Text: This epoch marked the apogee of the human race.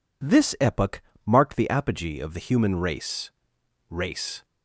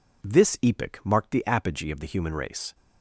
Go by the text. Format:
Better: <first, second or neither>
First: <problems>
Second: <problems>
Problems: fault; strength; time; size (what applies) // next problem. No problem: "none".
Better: second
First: pauses between "epoch" and "marked"; slight; at 1.0 s; 0.24 s long // says "race" twice; at 3.9 s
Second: none